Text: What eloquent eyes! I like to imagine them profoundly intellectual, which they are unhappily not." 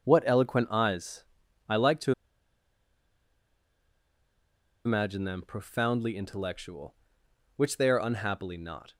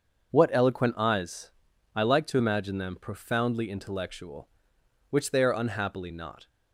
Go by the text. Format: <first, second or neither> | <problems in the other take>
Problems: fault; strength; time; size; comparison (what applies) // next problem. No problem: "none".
second | starts louder than the rest; until 1.1 s; 6.5 dB; also in the second // pauses between "to" and "imagine"; strong; at 2.1 s; 2.7 s long